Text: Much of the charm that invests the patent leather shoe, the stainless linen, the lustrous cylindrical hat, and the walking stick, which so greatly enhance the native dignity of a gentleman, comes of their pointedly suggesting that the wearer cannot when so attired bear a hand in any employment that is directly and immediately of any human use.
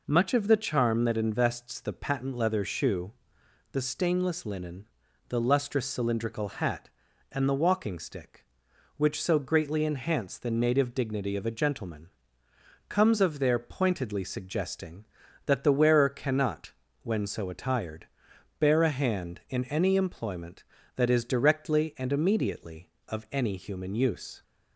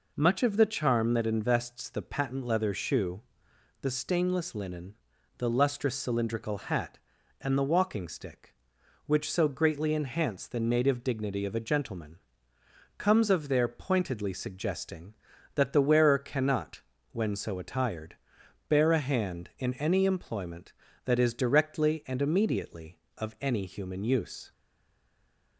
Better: first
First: pauses between "cannot" and "when"; slight; at 16.7 s; 0.32 s long // pauses between "attired" and "bear"; noticeable; at 18.0 s; 0.50 s long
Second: pauses between "cannot" and "when"; slight; at 16.8 s; 0.32 s long // pauses between "attired" and "bear"; noticeable; at 18.1 s; 0.50 s long // stays silent after the last word; from 24.5 s on; 1.0 s long

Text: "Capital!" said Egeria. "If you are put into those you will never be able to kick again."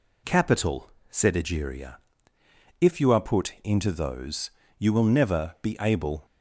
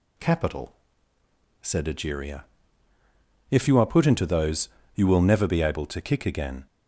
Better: second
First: pauses between "those" and "you"; slight; at 4.5 s; 0.28 s long // stops before "to kick again"; at 6.2 s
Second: pauses between "those" and "you"; slight; at 4.6 s; 0.24 s long

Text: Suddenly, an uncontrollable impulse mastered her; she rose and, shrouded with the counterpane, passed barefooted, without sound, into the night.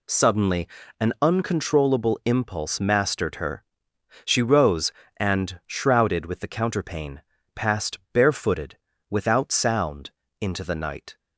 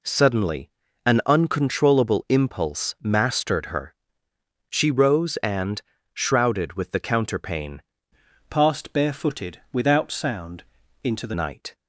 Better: first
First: none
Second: changes voice from "passed" to "the"; from 8.4 to 11.3 s; 2.9 s long

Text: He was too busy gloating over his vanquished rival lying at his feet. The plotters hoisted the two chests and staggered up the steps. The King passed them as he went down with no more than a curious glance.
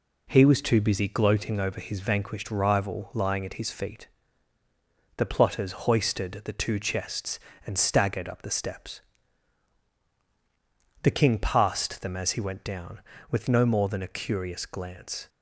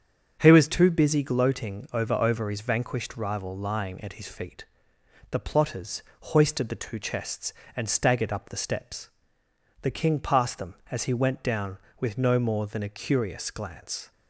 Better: first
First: pauses between "plotters" and "hoisted"; slight; at 5.7 s; 0.16 s long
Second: starts louder than the rest; strong; until 1.4 s; 7.5 dB // says "over" twice; at 2.1 s // pauses between "plotters" and "hoisted"; slight; at 6.0 s; 0.18 s long

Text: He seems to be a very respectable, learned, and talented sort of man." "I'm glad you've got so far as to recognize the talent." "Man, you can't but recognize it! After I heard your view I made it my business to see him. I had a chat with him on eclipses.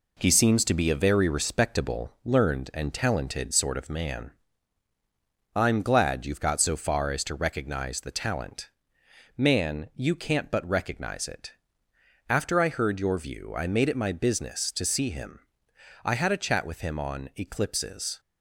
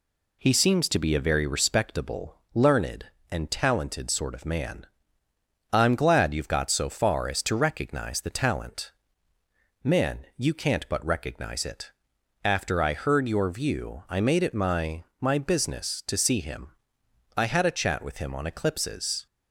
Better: first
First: none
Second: says "my" twice; at 15.1 s

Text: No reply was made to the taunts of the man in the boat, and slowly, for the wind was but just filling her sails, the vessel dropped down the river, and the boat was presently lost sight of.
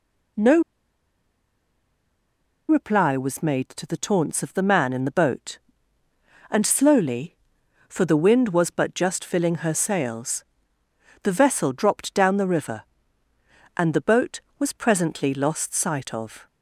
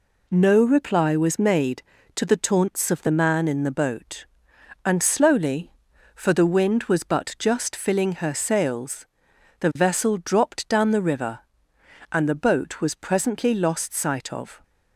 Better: second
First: pauses between "No" and "reply"; strong; at 0.6 s; 2.0 s long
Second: none

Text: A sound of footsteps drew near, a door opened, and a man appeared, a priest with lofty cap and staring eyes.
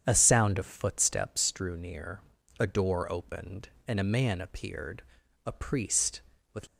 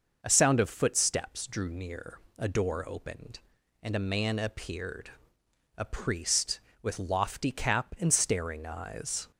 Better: second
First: starts louder than the rest; strong; until 1.0 s; 8.5 dB // stops before "lofty cap and staring eyes"; at 6.6 s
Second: none

